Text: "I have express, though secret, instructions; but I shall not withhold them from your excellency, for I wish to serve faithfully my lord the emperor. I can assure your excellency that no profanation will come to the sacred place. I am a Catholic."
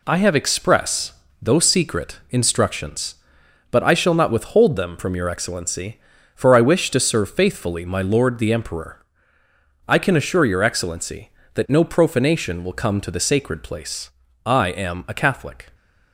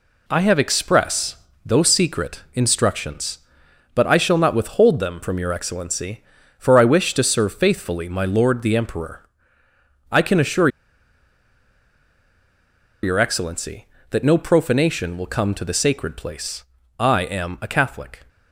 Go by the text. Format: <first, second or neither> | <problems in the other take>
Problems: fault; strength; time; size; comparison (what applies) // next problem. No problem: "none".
first | pauses between "assure" and "your"; strong; at 10.6 s; 2.3 s long